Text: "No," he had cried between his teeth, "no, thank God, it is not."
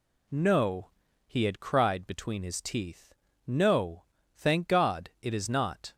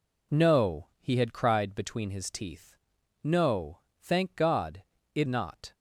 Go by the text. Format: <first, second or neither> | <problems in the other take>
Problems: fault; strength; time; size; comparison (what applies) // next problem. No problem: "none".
first | skips "is"; at 5.2 s